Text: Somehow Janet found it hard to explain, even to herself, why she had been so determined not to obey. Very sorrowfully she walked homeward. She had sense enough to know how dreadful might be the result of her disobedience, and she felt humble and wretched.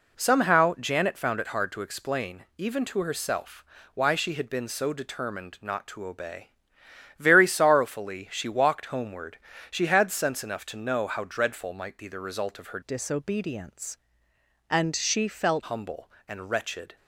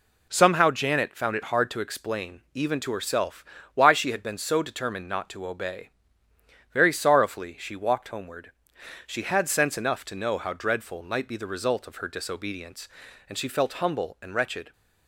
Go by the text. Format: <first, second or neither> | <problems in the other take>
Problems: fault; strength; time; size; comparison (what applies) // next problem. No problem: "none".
second | changes voice from "disobedience" to "felt"; from 12.8 to 15.6 s; 2.8 s long